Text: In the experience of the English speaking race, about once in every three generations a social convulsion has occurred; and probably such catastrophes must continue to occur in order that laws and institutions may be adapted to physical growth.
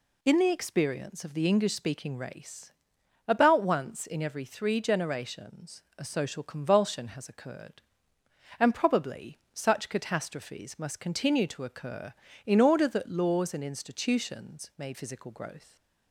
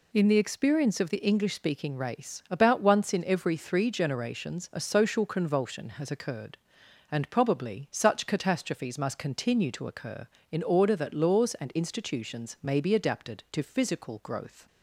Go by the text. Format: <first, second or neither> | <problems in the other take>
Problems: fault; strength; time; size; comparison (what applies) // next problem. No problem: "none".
second | pauses between "generations" and "a"; slight; at 5.8 s; 0.16 s long // pauses between "probably" and "such"; slight; at 9.3 s; 0.16 s long // skips "be adapted to"; at 14.9 s